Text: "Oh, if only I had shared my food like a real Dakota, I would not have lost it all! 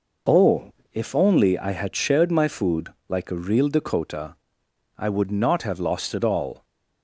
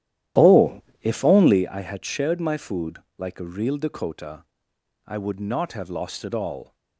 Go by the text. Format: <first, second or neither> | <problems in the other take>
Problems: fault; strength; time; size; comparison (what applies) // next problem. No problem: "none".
first | starts louder than the rest; strong; until 1.7 s; 12 dB // pauses between "food" and "like"; slight; at 2.9 s; 0.18 s long; slight in the first